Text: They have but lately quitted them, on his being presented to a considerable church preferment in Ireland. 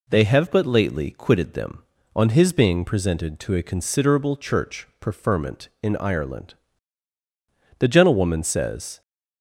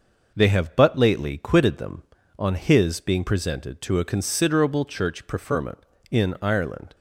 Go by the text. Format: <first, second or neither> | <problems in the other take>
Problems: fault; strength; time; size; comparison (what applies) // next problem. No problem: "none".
second | goes on to say "The gentlewoman says"; noticeable; from 7.7 s on; 1.2 s long